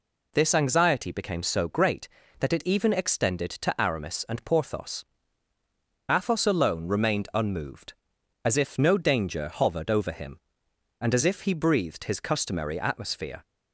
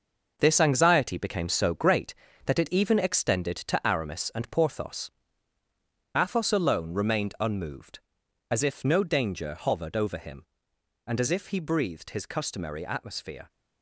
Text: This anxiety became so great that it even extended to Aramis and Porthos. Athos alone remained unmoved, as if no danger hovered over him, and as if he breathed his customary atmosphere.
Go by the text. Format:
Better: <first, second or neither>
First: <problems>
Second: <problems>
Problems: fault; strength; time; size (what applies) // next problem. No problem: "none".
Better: first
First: none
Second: gets quieter; strong; throughout; 8 dB